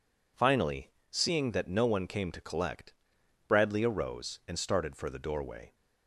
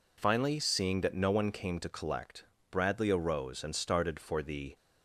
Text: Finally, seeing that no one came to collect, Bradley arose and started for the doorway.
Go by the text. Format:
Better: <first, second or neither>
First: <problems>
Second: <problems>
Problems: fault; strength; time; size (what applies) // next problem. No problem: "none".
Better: first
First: none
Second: stops before "doorway"; at 4.7 s